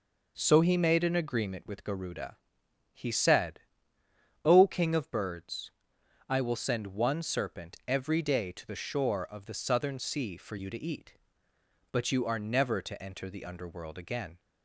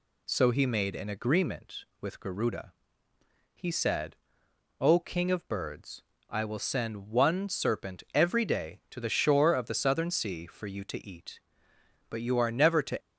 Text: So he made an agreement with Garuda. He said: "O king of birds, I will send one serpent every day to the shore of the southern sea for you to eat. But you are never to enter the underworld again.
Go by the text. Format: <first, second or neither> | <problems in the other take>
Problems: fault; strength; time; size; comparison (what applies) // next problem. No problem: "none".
first | stops before "enter the underworld again"; at 13.0 s